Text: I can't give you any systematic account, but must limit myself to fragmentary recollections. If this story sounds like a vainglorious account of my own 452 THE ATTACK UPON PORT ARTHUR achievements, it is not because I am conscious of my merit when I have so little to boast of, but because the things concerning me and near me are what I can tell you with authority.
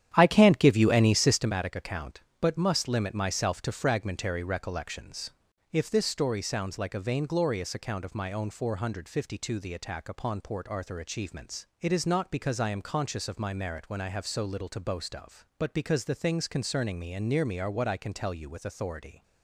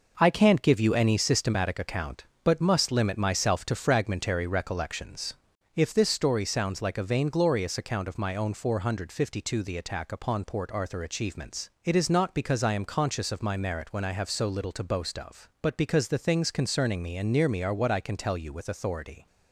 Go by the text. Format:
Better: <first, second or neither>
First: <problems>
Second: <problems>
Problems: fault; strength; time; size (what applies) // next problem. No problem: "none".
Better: second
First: starts louder than the rest; strong; until 1.5 s; 10 dB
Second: none